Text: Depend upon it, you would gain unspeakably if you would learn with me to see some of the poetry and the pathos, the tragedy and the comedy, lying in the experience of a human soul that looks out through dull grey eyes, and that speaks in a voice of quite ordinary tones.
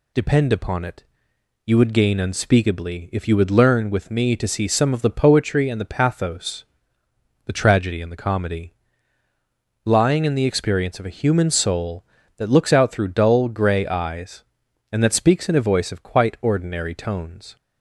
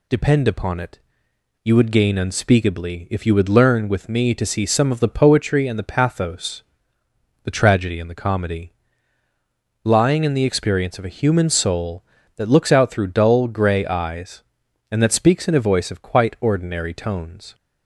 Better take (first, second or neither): neither